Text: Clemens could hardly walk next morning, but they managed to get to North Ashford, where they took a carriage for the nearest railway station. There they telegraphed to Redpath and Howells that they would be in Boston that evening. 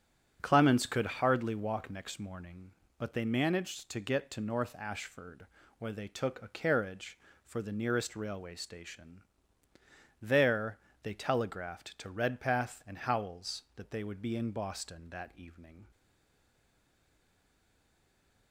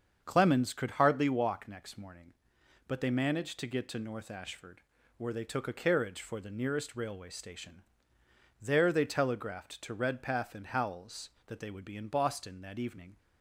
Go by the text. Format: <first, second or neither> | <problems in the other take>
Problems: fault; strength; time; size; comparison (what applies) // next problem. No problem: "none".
second | starts louder than the rest; strong; until 1.4 s; 9.5 dB; strong in the second // pauses between "There" and "they"; slight; at 10.7 s; 0.24 s long // stays silent after the last word; strong; from 15.9 s on; 2.6 s long